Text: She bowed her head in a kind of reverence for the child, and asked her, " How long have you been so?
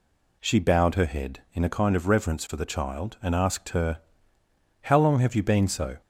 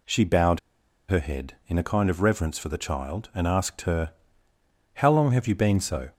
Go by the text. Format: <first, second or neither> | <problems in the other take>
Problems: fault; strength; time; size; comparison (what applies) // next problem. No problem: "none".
first | pauses between "bowed" and "her"; noticeable; at 0.5 s; 0.49 s long